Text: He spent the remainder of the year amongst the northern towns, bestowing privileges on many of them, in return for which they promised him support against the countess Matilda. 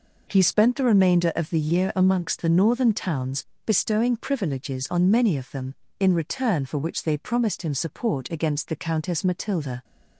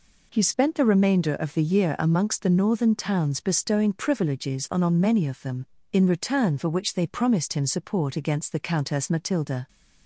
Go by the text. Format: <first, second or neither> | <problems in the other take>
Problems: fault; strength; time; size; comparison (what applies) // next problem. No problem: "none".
first | says "on" twice; at 4.8 s